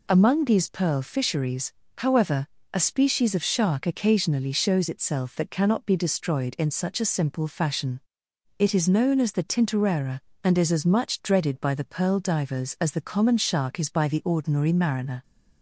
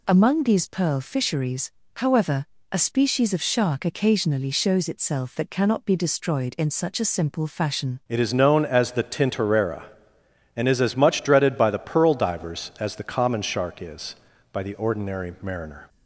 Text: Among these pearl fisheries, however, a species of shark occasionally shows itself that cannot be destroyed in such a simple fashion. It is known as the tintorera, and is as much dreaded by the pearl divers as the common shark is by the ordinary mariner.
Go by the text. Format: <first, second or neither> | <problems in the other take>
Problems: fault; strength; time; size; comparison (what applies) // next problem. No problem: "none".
first | changes voice at "It"; from 8.0 s on; 7.8 s long